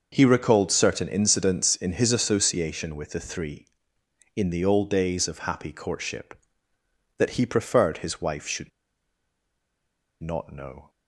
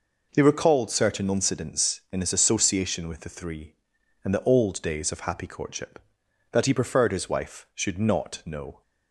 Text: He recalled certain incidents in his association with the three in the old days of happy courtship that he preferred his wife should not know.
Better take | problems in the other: second | starts louder than the rest; noticeable; until 1.1 s; 6 dB // pauses between "should" and "not"; strong; at 8.6 s; 1.5 s long

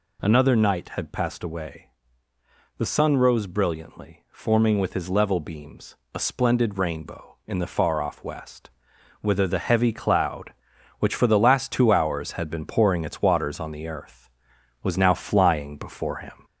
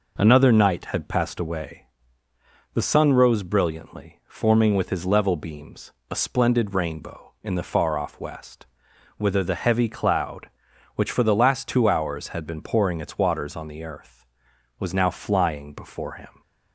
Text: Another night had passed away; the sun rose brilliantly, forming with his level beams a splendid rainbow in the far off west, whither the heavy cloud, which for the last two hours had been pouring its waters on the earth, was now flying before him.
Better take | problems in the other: second | gets louder; slight; throughout; 2.5 dB // pauses between "beams" and "a"; slight; at 5.9 s; 0.18 s long; slight in the second

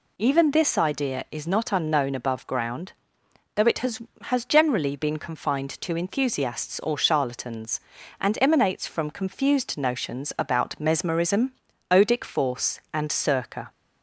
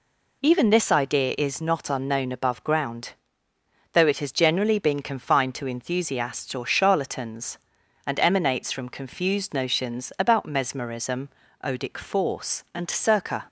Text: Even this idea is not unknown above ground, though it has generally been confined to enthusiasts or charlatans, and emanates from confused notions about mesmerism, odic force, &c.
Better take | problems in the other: second | says "has" twice; at 4.2 s

